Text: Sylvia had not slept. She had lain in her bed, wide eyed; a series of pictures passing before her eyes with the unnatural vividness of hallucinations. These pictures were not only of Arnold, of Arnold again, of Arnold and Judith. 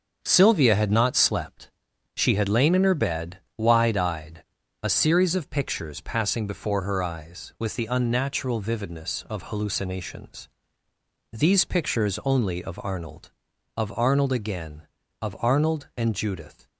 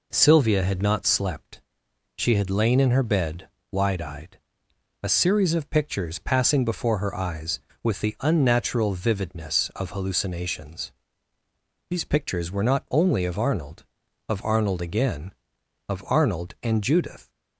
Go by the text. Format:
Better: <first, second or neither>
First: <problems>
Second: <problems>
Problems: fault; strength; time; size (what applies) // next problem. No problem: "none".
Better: second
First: starts louder than the rest; until 1.2 s; 7 dB // skips "were not"; at 12.2 s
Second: none